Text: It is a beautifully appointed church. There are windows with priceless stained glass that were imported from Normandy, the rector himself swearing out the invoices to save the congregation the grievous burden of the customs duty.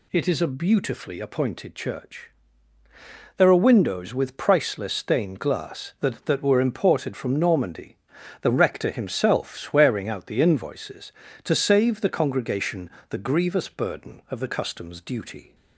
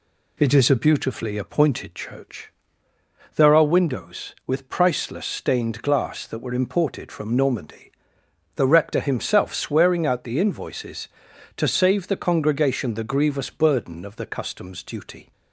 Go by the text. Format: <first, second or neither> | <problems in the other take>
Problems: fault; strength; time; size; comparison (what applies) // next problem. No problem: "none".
second | says "that" twice; at 6.2 s // pauses between "congregation" and "the"; slight; at 12.8 s; 0.22 s long